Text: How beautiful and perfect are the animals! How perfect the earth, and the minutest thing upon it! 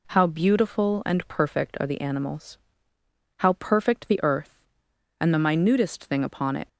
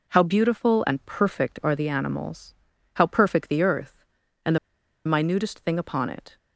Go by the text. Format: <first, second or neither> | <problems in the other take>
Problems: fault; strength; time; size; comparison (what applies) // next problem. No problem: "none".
first | pauses between "the" and "minutest"; noticeable; at 4.5 s; 0.48 s long